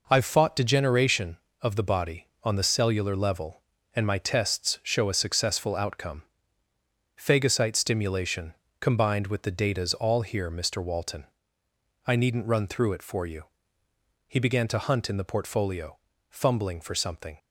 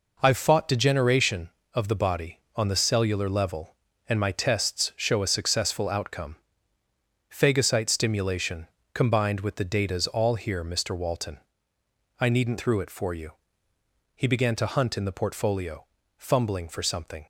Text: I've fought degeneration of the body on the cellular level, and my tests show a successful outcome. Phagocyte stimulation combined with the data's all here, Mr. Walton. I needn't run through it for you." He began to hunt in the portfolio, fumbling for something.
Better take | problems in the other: first | pauses between "stimulation" and "combined"; slight; at 8.6 s; 0.28 s long; slight in the first // skips "run"; at 12.5 s

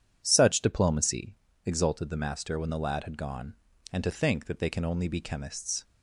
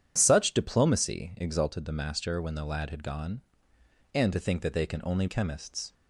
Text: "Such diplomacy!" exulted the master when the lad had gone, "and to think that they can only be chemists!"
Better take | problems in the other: first | starts louder than the rest; strong; until 1.1 s; 9.5 dB // skips "be"; at 5.2 s

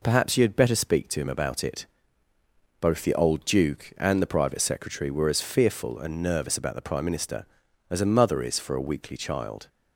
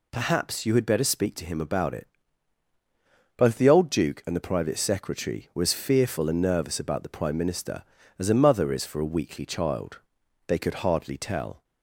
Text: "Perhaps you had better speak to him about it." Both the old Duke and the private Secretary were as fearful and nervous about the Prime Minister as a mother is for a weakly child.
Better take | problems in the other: first | goes on to say "They could hardly tell"; noticeable; from 10.4 s on; 1.1 s long

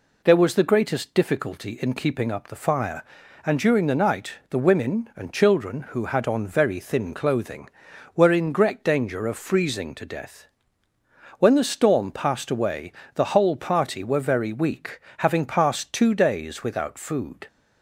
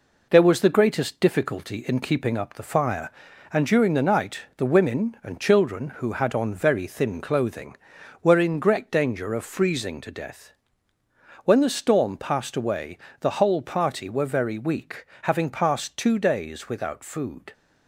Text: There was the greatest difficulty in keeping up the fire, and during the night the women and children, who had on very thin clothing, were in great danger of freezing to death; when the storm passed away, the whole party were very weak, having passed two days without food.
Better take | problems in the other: first | gets quieter; noticeable; throughout; 5 dB // pauses between "night" and "the"; slight; at 4.4 s; 0.18 s long; slight in the first

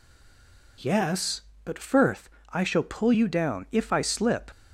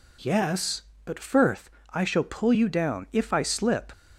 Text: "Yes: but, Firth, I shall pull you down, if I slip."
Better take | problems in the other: second | stays silent before the first word; slight; until 0.7 s; 0.7 s long

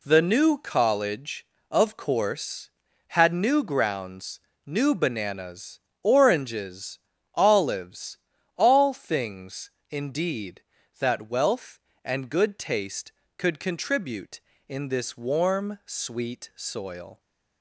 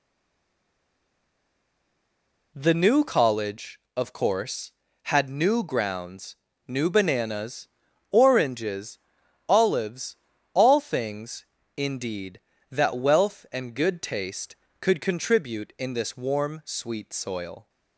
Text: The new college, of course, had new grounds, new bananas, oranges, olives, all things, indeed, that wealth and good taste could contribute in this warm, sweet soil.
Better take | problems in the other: first | stays silent before the first word; strong; until 2.5 s; 2.5 s long

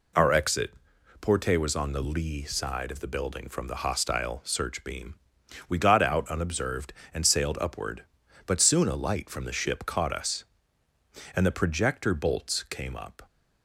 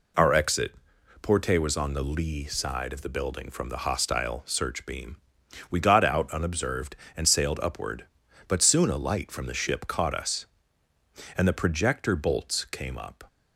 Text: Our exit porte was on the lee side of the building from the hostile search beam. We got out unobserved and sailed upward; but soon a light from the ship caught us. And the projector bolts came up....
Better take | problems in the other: neither | pauses between "exit" and "porte"; noticeable; the same in both

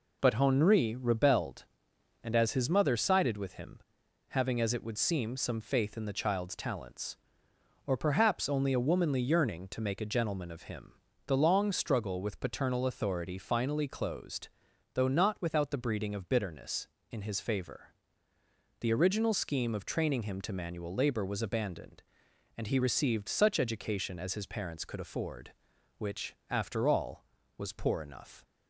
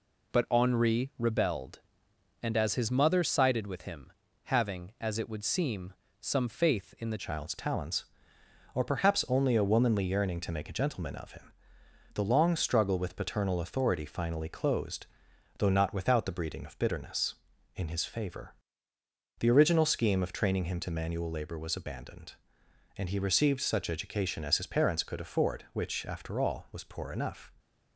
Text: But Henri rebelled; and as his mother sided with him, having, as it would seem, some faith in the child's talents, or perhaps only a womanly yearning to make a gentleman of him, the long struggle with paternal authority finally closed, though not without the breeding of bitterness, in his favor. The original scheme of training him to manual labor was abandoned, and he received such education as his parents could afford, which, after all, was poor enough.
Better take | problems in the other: first | changes voice at "child's"; from 7.1 s on; 20.4 s long

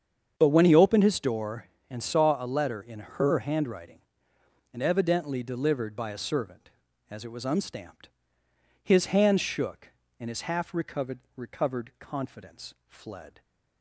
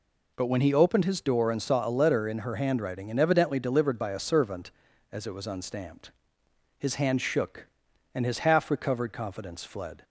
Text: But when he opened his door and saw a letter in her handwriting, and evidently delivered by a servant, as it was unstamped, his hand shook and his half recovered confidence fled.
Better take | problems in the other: second | starts louder than the rest; strong; until 1.3 s; 7.5 dB // says "recovered" twice; at 11.3 s

